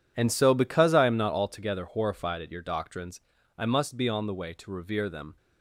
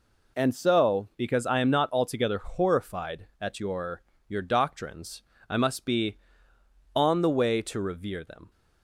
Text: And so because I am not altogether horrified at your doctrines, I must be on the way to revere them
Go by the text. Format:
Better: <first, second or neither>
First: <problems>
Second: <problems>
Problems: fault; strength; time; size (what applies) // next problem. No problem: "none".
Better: first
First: none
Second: says "your" twice; at 4.2 s